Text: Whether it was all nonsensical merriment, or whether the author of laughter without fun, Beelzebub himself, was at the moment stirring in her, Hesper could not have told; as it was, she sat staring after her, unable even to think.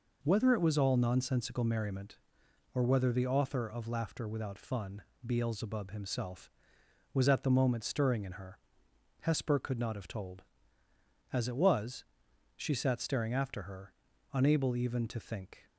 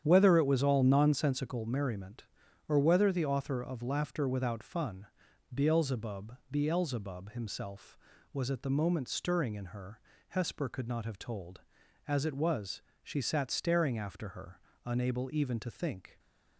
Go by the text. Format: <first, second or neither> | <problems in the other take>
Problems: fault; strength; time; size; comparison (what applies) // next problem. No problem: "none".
first | starts louder than the rest; strong; until 1.0 s; 9 dB // says "Beelzebub" twice; at 6.5 s